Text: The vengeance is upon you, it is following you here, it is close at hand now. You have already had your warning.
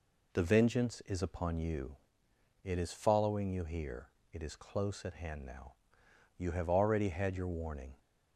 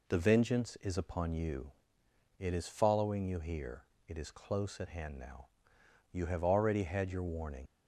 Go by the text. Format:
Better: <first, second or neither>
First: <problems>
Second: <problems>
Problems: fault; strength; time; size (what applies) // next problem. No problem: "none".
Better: first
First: none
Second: leaves "warning" unfinished; at 7.6 s; 80 ms